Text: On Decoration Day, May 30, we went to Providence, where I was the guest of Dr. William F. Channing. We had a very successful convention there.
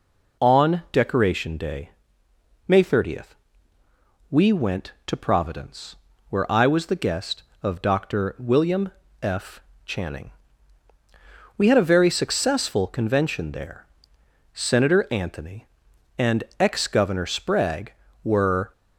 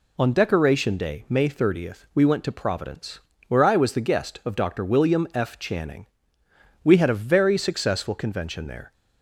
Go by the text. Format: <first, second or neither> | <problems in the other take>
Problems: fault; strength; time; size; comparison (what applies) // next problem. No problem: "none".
second | pauses between "William" and "F"; slight; at 8.9 s; 0.28 s long // goes on to say "Senator Anthony and ex Governor Sprague were"; strong; from 14.5 s on; 4.1 s long